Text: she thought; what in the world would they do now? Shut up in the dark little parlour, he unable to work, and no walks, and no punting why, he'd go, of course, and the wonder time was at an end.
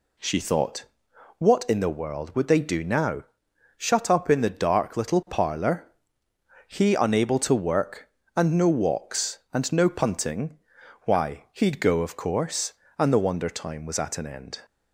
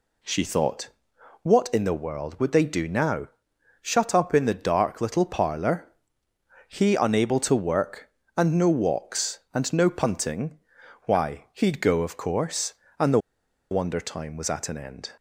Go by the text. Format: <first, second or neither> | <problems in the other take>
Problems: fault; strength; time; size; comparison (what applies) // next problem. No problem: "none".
first | pauses between "punting" and "why"; noticeable; at 10.5 s; 0.46 s long; noticeable in the first // pauses between "the" and "wonder"; noticeable; at 13.1 s; 0.52 s long